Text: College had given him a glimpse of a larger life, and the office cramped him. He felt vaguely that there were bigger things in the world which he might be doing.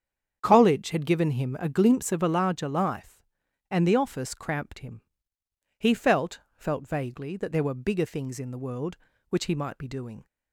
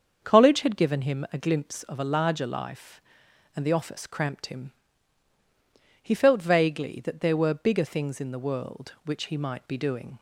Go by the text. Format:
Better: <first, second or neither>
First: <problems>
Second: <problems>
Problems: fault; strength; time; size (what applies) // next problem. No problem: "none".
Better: second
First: starts louder than the rest; strong; until 1.4 s; 8 dB // says "felt" twice; at 6.5 s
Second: starts louder than the rest; until 1.2 s; 7 dB